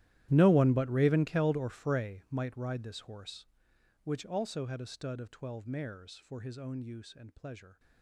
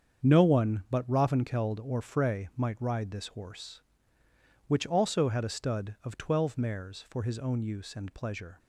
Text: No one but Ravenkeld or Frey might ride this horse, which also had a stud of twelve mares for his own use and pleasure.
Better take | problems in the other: second | gets quieter; strong; throughout; 21.5 dB // starts louder than the rest; strong; until 1.3 s; 13.5 dB; strong in the second

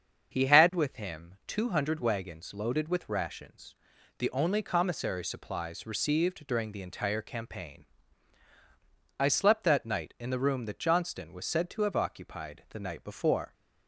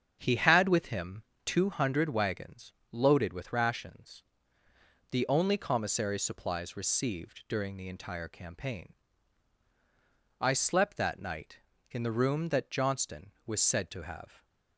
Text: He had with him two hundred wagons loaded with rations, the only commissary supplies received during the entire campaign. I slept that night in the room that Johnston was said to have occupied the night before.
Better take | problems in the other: first | starts louder than the rest; strong; until 1.2 s; 7.5 dB; also in the first // pauses between "him" and "two"; slight; at 1.2 s; 0.22 s long // pauses between "wagons" and "loaded"; slight; at 2.7 s; 0.18 s long // stops before "occupied the night before"; at 14.4 s

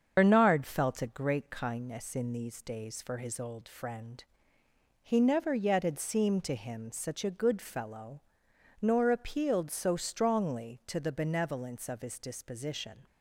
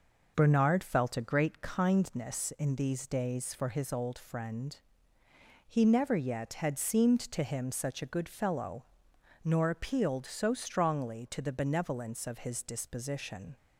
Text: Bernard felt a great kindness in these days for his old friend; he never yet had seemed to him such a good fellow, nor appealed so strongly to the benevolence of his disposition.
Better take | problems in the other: second | loses the start of "Bernard"; at 0.1 s; 70 ms // starts louder than the rest; until 1.1 s; 7 dB

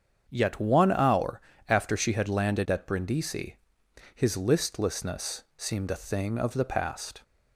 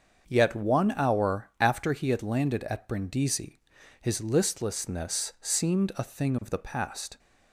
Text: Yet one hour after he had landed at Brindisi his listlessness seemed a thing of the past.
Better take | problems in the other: second | starts louder than the rest; strong; until 1.2 s; 7.5 dB; also in the second // pauses between "hour" and "after"; slight; at 1.4 s; 0.28 s long // says "she" for "he"; at 1.9 s // pauses between "Brindisi" and "his"; noticeable; at 3.5 s; 0.58 s long; also in the second // pauses between "listlessness" and "seemed"; slight; at 5.4 s; 0.16 s long

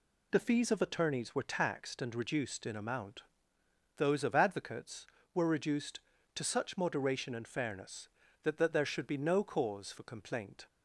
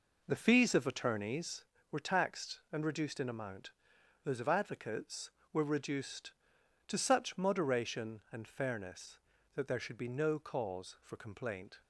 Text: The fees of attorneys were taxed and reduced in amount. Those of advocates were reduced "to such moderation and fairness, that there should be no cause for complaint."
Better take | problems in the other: second | says "that" twice; at 8.5 s

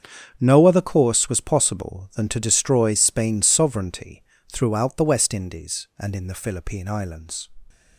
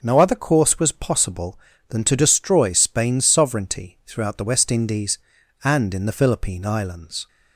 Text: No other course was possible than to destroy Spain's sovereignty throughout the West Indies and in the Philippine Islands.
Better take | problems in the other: second | gets quieter; strong; throughout; 13.5 dB // pauses between "sovereignty" and "throughout"; slight; at 4.2 s; 0.28 s long

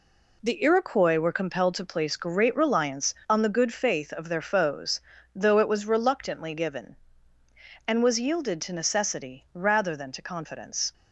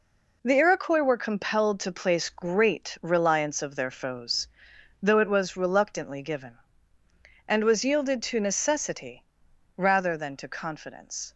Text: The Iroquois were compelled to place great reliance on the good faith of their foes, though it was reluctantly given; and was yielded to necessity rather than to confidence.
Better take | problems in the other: first | skips "on the good faith"; at 3.6 s // pauses between "necessity" and "rather"; noticeable; at 9.2 s; 0.50 s long

